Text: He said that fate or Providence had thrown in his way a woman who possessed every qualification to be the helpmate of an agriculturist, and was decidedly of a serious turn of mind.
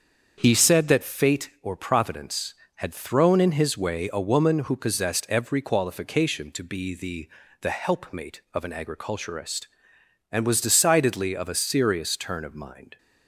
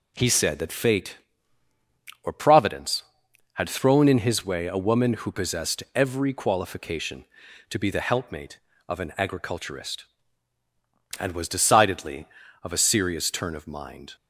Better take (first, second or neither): second